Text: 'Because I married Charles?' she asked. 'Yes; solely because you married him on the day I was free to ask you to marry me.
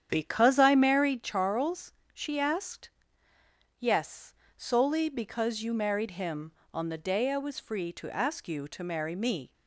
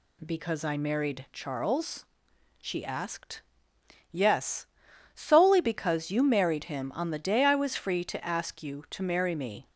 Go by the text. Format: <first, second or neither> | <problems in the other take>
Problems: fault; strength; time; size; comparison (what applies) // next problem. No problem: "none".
second | starts louder than the rest; strong; until 1.2 s; 9 dB